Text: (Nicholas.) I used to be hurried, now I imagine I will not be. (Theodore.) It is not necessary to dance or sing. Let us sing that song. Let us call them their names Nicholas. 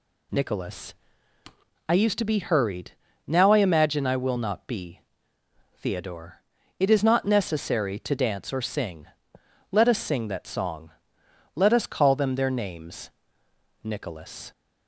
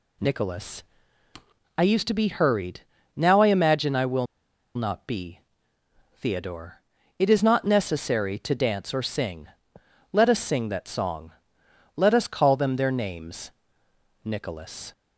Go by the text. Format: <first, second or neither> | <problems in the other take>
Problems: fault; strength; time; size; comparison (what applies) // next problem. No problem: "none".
first | pauses between "will" and "not"; noticeable; at 4.2 s; 0.49 s long // pauses between "names" and "Nicholas"; noticeable; at 13.4 s; 0.76 s long; noticeable in the first